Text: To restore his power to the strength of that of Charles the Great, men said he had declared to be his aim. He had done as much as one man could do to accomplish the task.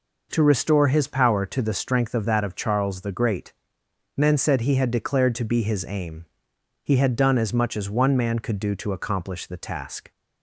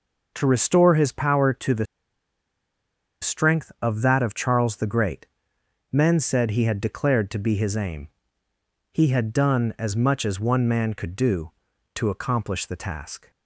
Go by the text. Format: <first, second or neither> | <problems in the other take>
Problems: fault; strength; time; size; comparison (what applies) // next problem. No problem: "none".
first | pauses between "the" and "strength"; strong; at 1.8 s; 1.3 s long